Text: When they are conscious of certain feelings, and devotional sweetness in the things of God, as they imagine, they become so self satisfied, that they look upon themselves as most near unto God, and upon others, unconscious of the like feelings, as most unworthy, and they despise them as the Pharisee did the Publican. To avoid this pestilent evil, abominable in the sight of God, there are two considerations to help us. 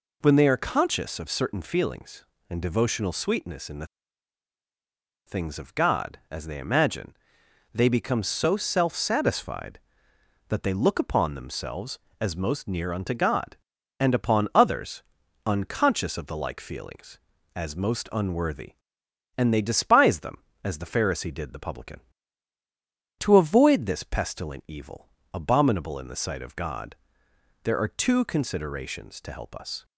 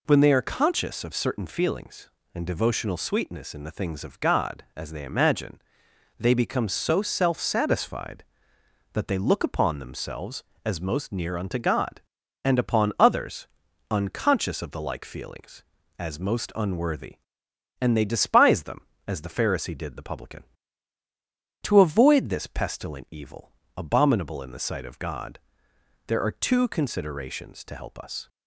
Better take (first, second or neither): second